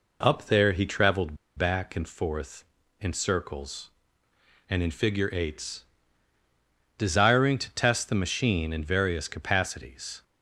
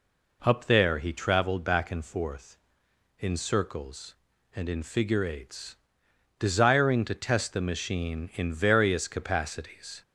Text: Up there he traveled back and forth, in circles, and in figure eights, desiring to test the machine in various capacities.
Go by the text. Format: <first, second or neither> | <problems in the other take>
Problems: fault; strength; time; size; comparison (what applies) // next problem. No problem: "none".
second | pauses between "traveled" and "back"; slight; at 1.3 s; 0.22 s long